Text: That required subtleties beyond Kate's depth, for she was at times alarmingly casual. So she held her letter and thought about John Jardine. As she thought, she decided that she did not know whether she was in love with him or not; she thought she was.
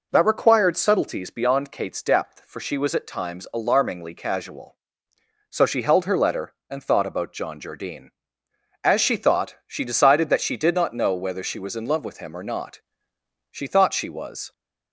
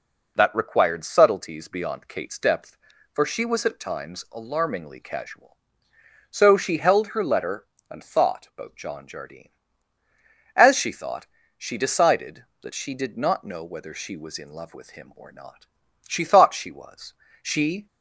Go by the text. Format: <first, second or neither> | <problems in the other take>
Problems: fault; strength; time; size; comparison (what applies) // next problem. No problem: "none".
first | goes on to say "She"; slight; from 17.4 s on; 0.46 s long